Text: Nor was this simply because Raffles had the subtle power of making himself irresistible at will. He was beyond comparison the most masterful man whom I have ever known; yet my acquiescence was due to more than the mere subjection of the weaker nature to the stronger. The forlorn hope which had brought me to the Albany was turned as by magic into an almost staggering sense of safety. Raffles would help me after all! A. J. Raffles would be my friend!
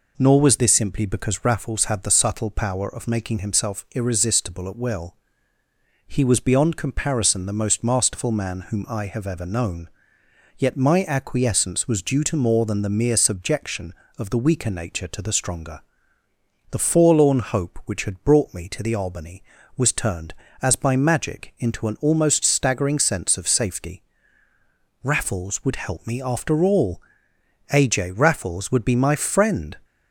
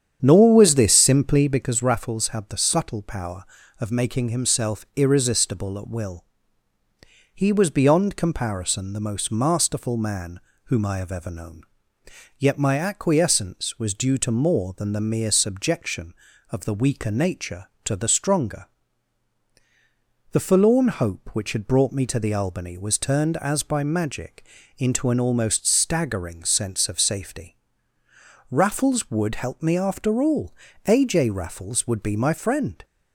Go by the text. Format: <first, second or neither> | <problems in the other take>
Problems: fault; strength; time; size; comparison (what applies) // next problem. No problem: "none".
first | starts louder than the rest; strong; until 1.6 s; 8.5 dB // pauses between "man" and "whom"; slight; at 10.3 s; 0.24 s long // pauses between "magic" and "into"; slight; at 24.4 s; 0.32 s long